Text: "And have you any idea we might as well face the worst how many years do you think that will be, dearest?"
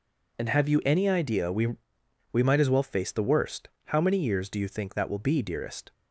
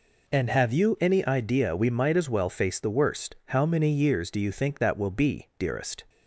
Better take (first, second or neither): second